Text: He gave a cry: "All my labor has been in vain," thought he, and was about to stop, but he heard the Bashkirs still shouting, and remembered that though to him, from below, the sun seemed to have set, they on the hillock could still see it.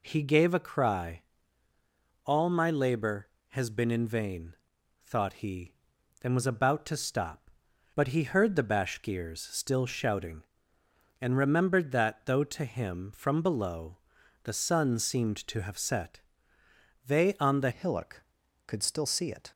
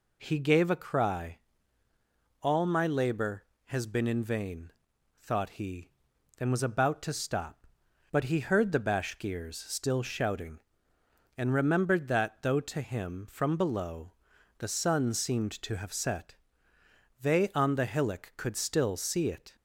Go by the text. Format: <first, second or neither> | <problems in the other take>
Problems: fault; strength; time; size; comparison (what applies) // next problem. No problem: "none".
second | changes voice at "hillock"; from 17.7 s on; 1.8 s long